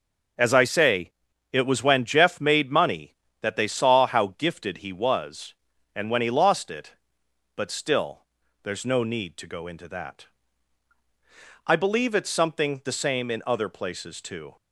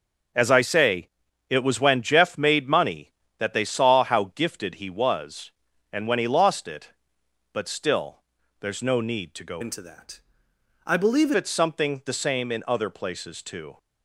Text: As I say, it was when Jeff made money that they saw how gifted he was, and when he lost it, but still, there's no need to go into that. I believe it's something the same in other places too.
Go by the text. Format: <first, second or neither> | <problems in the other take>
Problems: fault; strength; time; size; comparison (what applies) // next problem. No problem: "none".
first | changes voice from "into" to "believe"; from 9.6 to 11.3 s; 1.7 s long